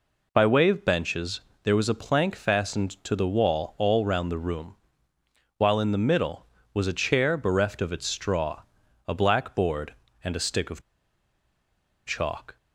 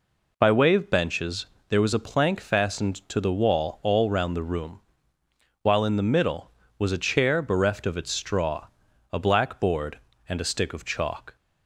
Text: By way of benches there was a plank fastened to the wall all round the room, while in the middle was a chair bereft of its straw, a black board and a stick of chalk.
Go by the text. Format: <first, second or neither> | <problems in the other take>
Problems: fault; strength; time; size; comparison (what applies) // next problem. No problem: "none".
second | pauses between "benches" and "there"; slight; at 1.4 s; 0.22 s long; slight in the second // pauses between "of" and "chalk"; strong; at 10.8 s; 1.2 s long